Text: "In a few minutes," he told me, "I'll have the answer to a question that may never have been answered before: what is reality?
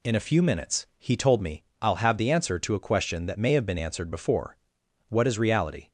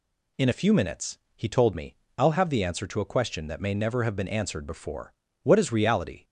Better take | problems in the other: second | skips "never"; at 3.5 s

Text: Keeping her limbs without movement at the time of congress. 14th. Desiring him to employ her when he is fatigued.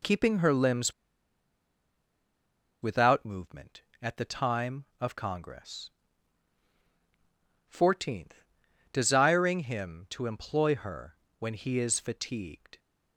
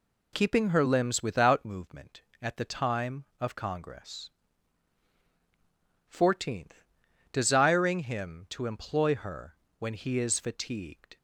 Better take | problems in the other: second | pauses between "limbs" and "without"; strong; at 0.9 s; 1.8 s long // pauses between "her" and "when"; slight; at 11.1 s; 0.22 s long; slight in the second

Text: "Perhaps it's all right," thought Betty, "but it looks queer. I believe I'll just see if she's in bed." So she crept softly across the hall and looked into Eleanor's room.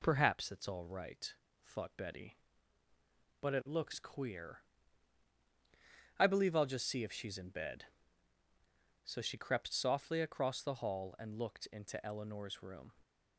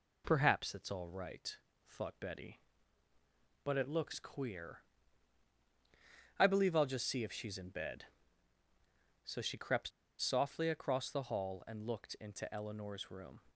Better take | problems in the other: first | pauses between "crept" and "softly"; slight; at 9.9 s; 0.31 s long

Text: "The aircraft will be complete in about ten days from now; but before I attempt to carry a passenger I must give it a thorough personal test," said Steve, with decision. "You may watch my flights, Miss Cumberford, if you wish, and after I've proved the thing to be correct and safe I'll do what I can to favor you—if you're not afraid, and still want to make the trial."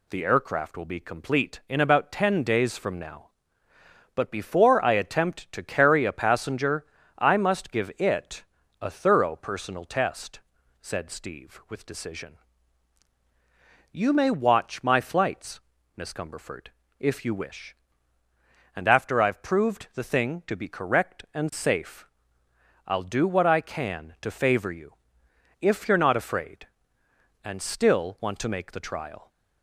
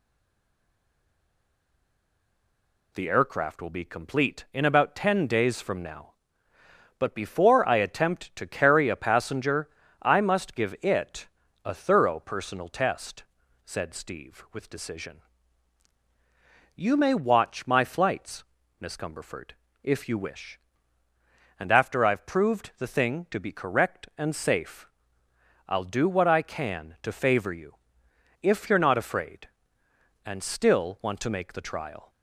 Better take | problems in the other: first | stays silent before the first word; strong; until 2.9 s; 2.9 s long // pauses between "passenger" and "I"; slight; at 9.6 s; 0.32 s long; slight in the first // pauses between "it" and "a"; slight; at 11.2 s; 0.36 s long; slight in the first // pauses between "safe" and "I'll"; noticeable; at 24.8 s; 0.80 s long; noticeable in the first

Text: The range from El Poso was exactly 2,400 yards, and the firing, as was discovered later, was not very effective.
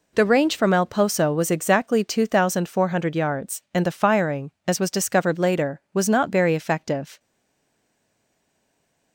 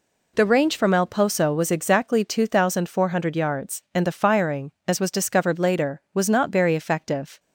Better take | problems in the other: second | stays silent after the last word; noticeable; from 7.1 s on; 2.0 s long

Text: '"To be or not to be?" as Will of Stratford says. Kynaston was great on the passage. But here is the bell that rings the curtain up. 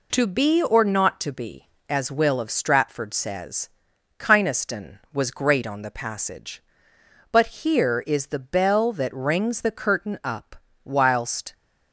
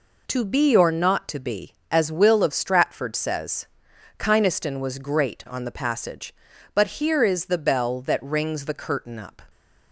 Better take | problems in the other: second | goes on to say "Whilst"; noticeable; from 10.8 s on; 0.70 s long

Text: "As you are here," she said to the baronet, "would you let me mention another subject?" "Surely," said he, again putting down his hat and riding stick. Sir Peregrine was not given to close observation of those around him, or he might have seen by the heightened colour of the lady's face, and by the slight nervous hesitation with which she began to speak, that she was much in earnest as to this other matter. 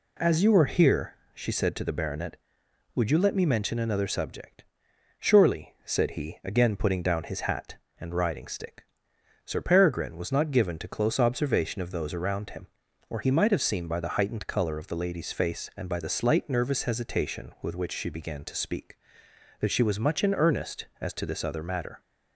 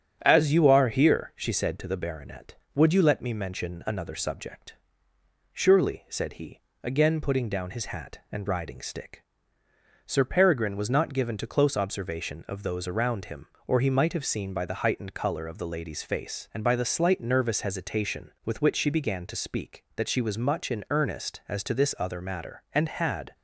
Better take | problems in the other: first | starts louder than the rest; strong; until 1.2 s; 8.5 dB // goes on to say "And had"; noticeable; from 22.7 s on; 0.62 s long

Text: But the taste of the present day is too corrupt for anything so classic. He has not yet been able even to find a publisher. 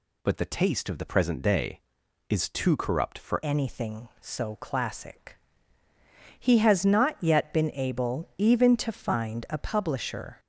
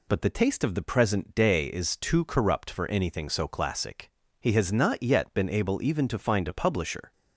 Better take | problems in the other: second | changes voice at "anything"; from 3.4 s on; 6.9 s long

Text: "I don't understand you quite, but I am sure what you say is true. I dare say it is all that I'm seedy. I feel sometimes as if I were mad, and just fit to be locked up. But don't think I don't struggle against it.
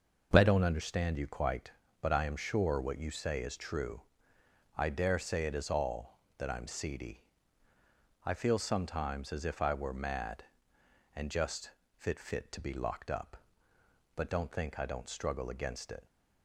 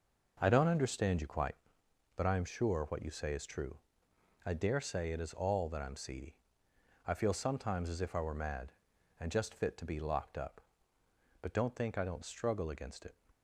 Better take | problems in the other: second | starts louder than the rest; until 1.3 s; 6 dB // pauses between "just" and "fit"; slight; at 11.7 s; 0.26 s long // says "fit" twice; at 12.1 s

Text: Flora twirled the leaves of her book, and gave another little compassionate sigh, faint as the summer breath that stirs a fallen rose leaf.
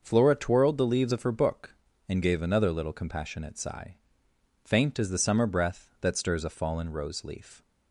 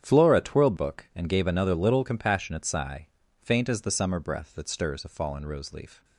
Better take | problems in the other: first | starts louder than the rest; strong; until 1.0 s; 9 dB; also in the first // skips "the leaves of her"; at 0.7 s

